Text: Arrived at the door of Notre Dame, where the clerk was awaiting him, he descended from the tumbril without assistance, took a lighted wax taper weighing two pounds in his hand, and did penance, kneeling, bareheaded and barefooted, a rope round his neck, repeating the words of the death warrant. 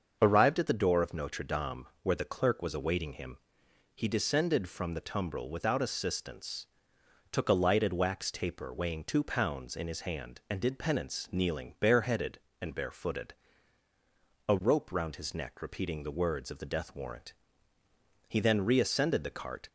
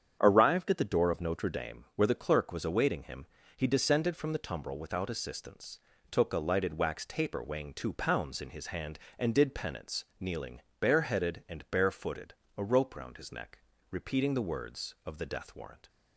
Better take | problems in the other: second | starts louder than the rest; until 1.2 s; 6.5 dB; strong in the second // goes on to say "He then reascended the cart"; from 18.2 s on; 1.4 s long

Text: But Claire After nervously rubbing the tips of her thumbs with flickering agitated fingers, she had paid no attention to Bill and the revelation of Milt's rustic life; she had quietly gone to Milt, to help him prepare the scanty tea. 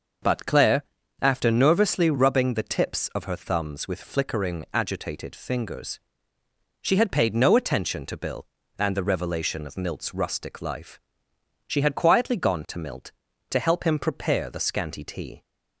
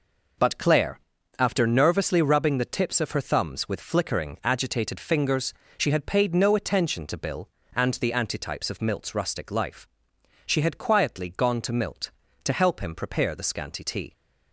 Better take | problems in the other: first | pauses between "Claire" and "After"; at 0.9 s; 0.38 s long; also in the first // says "antitypes" for "revelation"; at 8.1 s

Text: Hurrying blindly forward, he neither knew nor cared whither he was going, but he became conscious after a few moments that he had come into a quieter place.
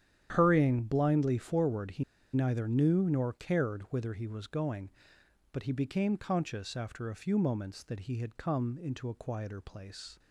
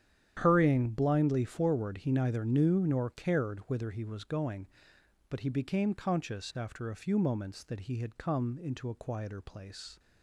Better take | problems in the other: second | starts louder than the rest; strong; until 1.3 s; 10 dB; strong in the second // pauses between "he" and "neither"; slight; at 2.0 s; 0.31 s long

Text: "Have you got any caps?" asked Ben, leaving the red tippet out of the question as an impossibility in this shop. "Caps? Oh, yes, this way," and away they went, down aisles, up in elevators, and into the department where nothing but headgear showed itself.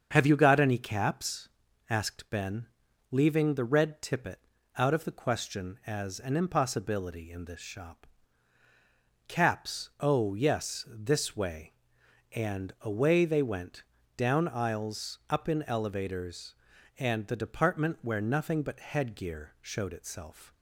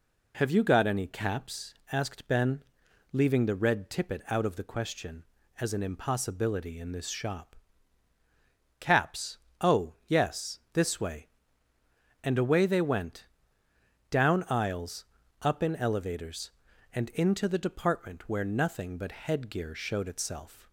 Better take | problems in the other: second | starts louder than the rest; strong; until 1.1 s; 7 dB // pauses between "tippet" and "out"; slight; at 4.4 s; 0.30 s long // skips "into"; at 17.2 s

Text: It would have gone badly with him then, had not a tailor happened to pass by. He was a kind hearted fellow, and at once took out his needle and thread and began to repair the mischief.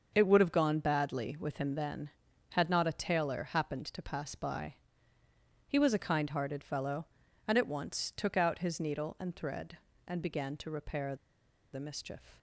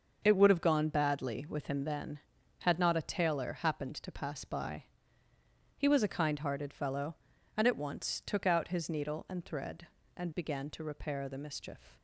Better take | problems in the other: second | starts louder than the rest; until 1.1 s; 6.5 dB; also in the second // pauses between "repair" and "the"; noticeable; at 11.1 s; 0.58 s long

